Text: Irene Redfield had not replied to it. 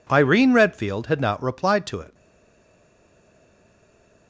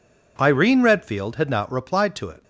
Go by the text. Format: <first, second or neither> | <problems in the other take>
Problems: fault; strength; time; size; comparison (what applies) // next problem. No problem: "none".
second | stays silent after the last word; from 2.1 s on; 2.1 s long